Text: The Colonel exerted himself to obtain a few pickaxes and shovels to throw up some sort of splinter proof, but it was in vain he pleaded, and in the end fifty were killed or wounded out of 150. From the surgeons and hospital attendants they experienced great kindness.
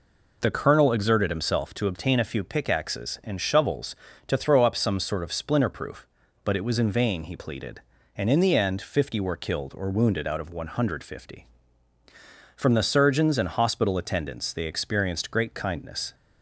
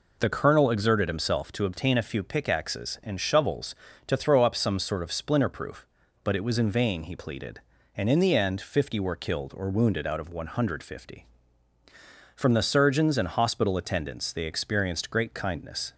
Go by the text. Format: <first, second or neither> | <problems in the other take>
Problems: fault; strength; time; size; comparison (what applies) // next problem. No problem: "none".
neither | none